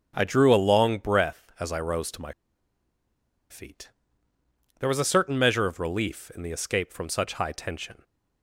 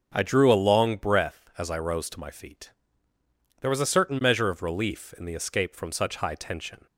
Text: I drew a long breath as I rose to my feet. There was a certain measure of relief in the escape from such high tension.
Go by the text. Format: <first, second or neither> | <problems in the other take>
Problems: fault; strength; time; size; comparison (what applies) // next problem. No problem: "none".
second | starts louder than the rest; until 1.1 s; 6.5 dB; also in the second // pauses between "my" and "feet"; at 2.3 s; 1.1 s long